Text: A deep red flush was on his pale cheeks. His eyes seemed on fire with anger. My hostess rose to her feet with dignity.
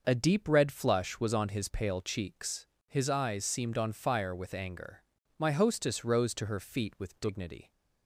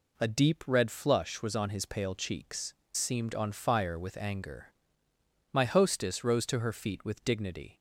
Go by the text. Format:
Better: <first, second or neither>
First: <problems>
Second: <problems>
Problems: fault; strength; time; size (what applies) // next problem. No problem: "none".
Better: first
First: none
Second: skips "His eyes"; at 2.8 s